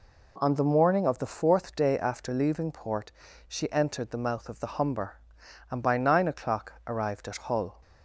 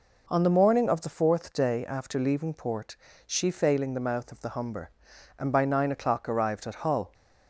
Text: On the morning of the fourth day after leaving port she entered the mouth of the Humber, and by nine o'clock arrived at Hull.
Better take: first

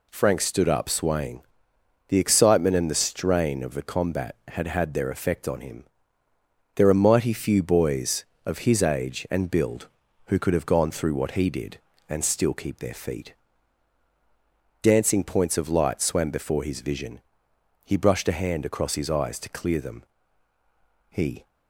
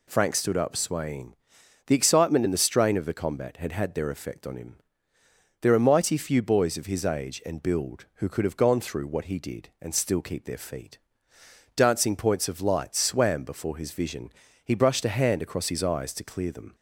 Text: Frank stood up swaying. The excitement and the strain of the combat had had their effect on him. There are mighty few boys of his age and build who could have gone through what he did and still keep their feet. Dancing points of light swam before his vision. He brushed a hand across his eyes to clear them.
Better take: second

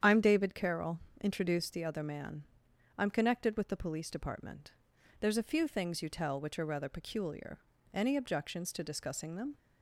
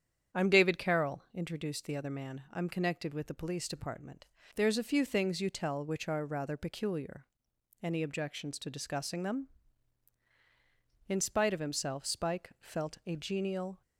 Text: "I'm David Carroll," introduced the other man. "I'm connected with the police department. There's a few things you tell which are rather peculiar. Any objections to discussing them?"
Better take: first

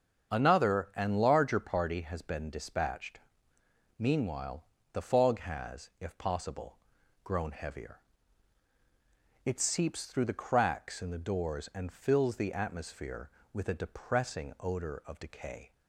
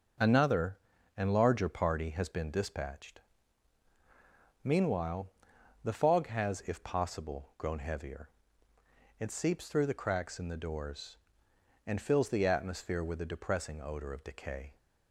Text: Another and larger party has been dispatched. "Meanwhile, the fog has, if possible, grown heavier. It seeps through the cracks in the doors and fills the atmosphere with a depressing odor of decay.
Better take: neither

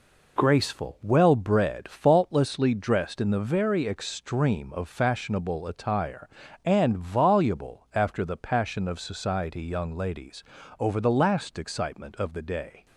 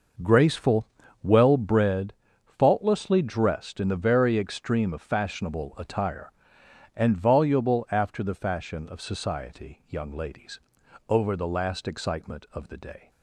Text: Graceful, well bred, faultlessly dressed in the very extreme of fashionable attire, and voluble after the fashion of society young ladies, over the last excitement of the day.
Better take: second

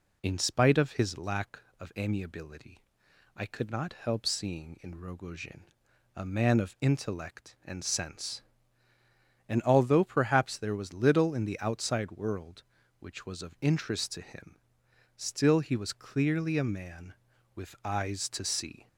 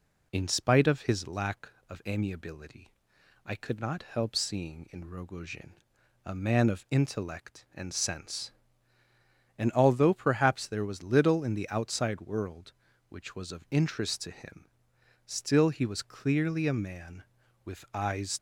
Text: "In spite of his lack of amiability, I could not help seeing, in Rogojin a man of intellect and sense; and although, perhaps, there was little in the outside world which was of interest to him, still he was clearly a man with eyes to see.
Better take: first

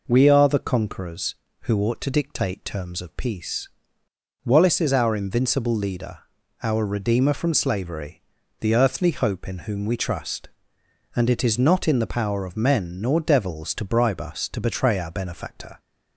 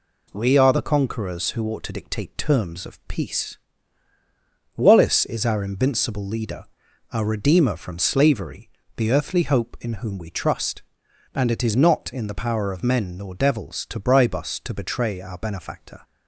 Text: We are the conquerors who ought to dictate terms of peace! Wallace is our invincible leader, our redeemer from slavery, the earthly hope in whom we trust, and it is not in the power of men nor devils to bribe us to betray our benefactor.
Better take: neither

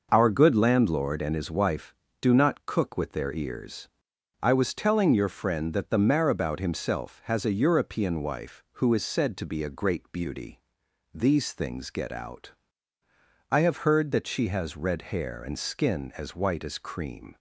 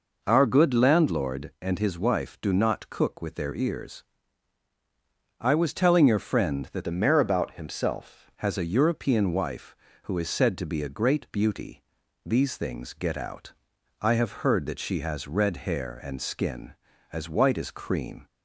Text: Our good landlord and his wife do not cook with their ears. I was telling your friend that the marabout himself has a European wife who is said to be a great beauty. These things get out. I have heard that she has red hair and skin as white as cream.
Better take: first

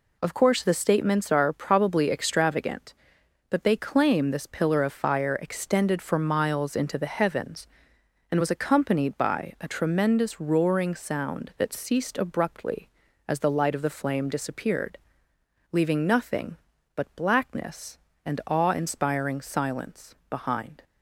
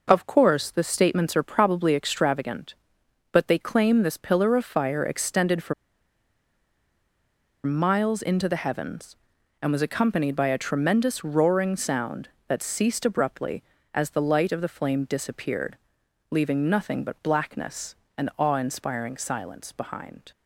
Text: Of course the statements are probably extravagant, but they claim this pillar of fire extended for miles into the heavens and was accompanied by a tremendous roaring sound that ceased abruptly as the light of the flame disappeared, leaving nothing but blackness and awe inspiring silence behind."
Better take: first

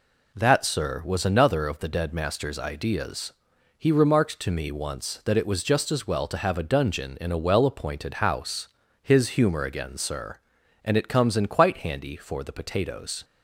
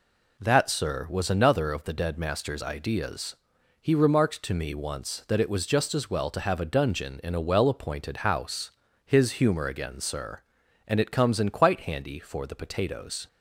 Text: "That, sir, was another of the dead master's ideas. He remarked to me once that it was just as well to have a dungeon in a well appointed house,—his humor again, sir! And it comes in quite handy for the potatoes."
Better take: neither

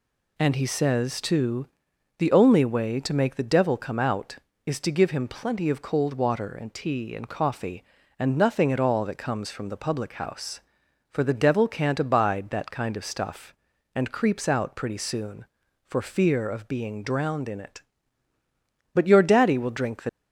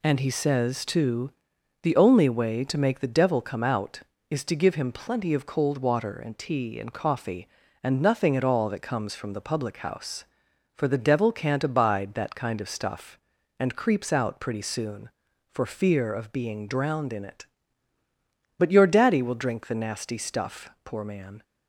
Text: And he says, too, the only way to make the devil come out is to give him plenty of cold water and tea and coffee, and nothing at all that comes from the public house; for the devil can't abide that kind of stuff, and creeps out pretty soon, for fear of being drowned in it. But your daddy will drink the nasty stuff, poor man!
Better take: second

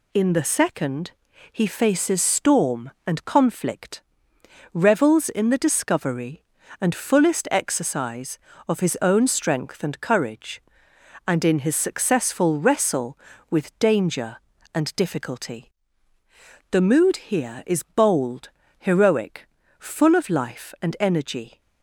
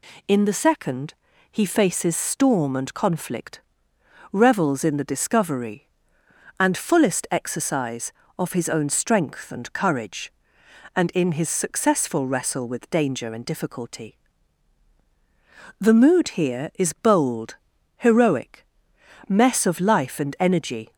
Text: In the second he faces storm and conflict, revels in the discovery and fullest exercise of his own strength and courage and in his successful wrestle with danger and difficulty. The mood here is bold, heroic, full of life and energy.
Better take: first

